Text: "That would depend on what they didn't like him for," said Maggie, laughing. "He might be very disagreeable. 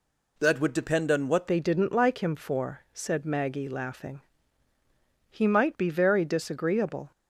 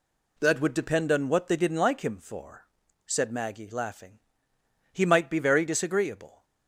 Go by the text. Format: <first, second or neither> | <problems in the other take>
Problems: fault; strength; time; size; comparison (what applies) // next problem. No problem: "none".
second | changes voice at "they"; from 1.4 s on; 5.7 s long